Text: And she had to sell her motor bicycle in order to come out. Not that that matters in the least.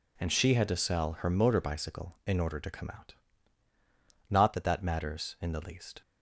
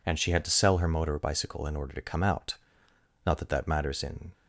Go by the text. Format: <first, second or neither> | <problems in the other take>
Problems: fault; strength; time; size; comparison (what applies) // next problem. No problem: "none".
first | stops before "the least"; at 4.3 s